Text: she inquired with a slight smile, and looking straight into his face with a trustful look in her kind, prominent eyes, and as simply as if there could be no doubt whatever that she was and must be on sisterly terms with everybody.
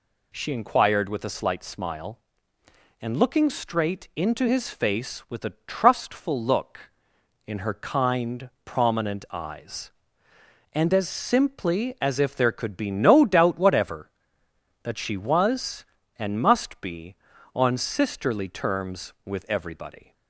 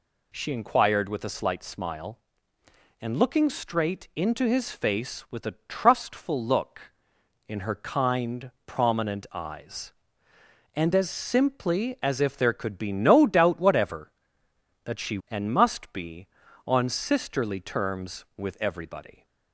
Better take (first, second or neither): first